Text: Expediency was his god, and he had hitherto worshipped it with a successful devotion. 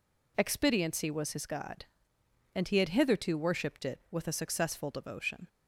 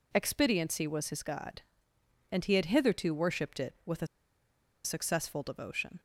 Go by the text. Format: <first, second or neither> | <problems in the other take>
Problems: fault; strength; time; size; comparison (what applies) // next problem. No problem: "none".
first | pauses between "a" and "successful"; noticeable; at 4.0 s; 0.78 s long